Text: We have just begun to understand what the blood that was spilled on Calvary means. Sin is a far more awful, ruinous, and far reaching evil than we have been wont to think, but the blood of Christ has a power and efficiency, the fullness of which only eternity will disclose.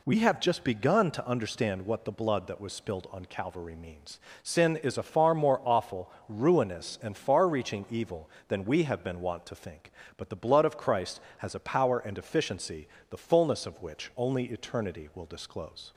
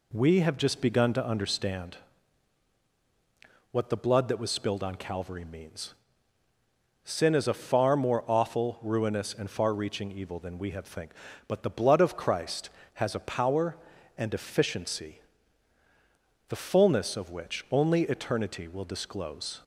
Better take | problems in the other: first | pauses between "understand" and "what"; strong; at 1.9 s; 1.7 s long // skips "been wont to"; at 10.8 s

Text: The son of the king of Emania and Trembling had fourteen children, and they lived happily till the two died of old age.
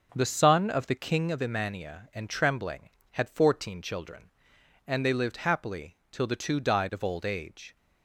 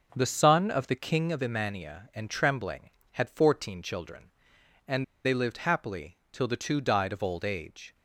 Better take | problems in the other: first | starts louder than the rest; noticeable; until 1.1 s; 6 dB; noticeable in the first // pauses between "and" and "they"; slight; at 5.0 s; 0.21 s long

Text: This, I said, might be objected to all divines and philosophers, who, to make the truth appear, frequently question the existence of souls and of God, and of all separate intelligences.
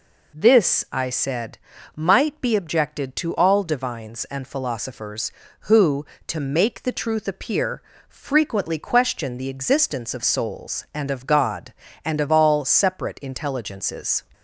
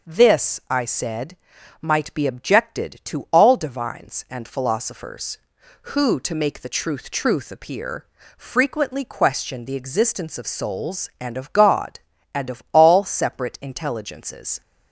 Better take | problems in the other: first | says "truth" twice; at 7.0 s

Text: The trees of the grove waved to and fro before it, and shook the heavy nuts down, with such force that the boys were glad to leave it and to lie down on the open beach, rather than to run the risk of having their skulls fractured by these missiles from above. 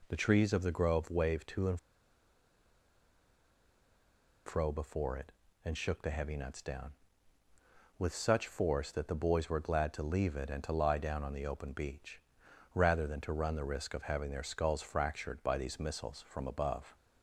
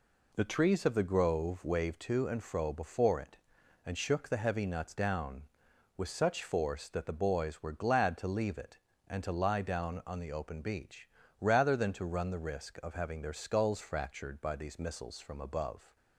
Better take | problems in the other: second | pauses between "and" and "fro"; strong; at 1.7 s; 2.6 s long

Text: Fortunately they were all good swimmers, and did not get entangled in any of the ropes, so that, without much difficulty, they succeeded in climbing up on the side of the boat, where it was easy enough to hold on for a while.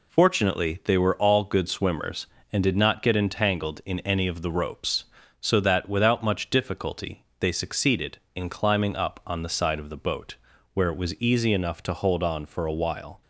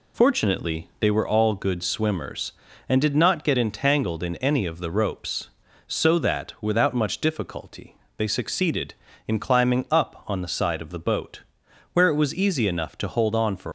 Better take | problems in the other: first | stops before "a while"; at 13.6 s

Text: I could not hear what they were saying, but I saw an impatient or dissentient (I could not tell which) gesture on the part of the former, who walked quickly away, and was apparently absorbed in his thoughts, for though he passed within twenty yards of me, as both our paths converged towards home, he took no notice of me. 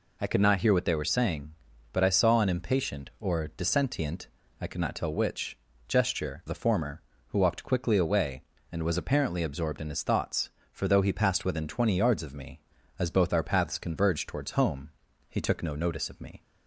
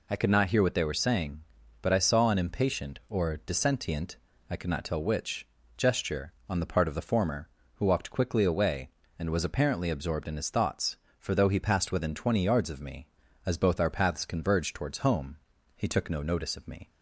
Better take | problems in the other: second | skips "on the part of"; at 6.4 s

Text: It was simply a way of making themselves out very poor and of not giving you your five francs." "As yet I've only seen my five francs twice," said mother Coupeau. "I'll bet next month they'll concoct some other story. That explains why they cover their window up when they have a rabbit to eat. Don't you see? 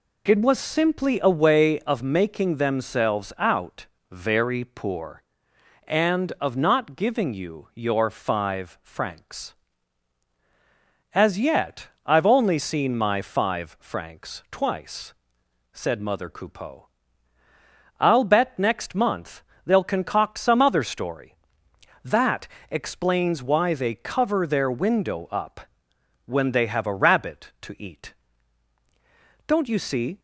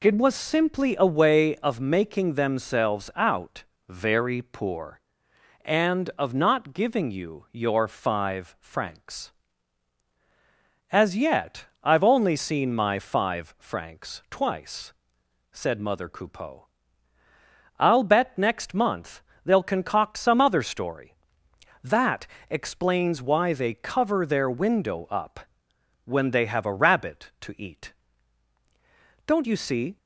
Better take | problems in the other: neither | pauses between "out" and "very"; slight; the same in both // pauses between "yet" and "I've"; slight; the same in both // pauses between "month" and "they'll"; slight; the same in both // pauses between "That" and "explains"; slight; the same in both // pauses between "up" and "when"; noticeable; the same in both

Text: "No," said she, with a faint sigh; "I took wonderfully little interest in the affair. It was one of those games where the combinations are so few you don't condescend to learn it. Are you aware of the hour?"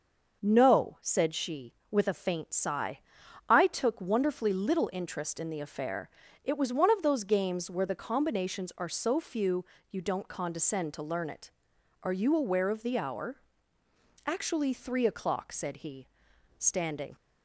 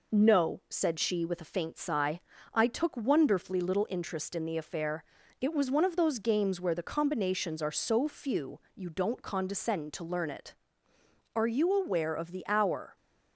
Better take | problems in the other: second | pauses between "few" and "you"; slight; at 9.6 s; 0.28 s long // goes on to say "Actually three o'clock said he standing"; strong; from 14.2 s on; 2.9 s long

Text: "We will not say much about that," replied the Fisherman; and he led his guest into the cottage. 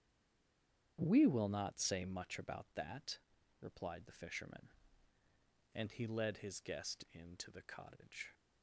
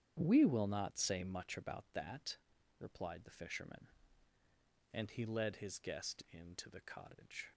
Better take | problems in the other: second | stays silent before the first word; slight; until 0.9 s; 0.9 s long // starts louder than the rest; strong; until 2.0 s; 9 dB; strong in the second

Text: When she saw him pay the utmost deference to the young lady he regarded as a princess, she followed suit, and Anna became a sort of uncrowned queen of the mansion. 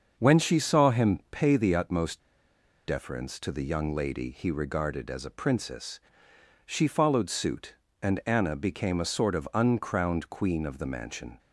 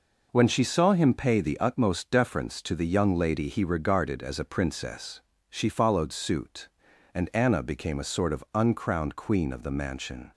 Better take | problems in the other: second | starts louder than the rest; until 1.1 s; 6.5 dB // pauses between "utmost" and "deference"; noticeable; at 2.2 s; 0.66 s long

